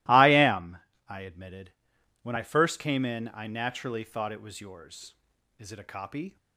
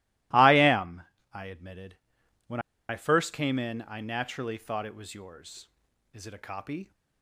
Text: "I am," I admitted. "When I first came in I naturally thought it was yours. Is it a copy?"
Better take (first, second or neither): first